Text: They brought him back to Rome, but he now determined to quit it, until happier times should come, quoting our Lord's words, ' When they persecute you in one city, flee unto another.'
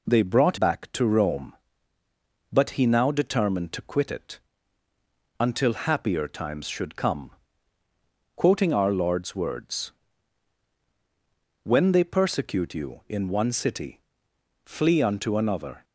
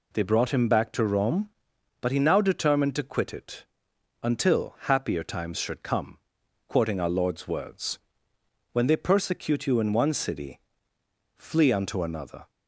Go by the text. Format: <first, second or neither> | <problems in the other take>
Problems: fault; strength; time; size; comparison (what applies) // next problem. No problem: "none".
second | skips "him"; at 0.5 s